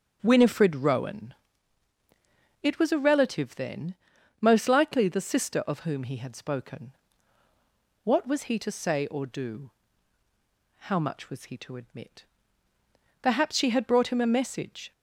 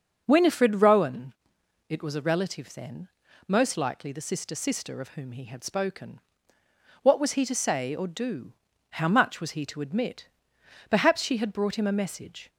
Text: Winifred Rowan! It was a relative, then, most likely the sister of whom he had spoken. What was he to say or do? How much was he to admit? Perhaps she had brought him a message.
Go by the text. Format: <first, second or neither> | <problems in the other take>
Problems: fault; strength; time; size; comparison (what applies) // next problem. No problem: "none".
first | starts louder than the rest; until 1.2 s; 7 dB; strong in the first // says "sister" twice; at 4.5 s